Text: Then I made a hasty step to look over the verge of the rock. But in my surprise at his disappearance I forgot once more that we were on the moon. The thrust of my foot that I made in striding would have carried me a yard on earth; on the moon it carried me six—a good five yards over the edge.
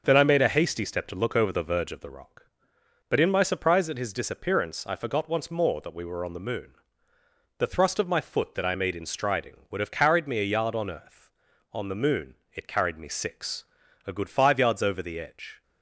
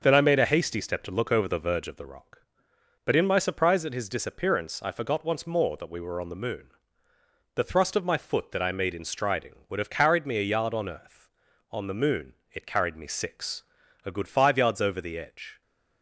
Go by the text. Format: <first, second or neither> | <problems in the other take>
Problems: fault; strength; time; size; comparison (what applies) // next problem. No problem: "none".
neither | starts louder than the rest; the same in both // pauses between "moon" and "it"; slight; the same in both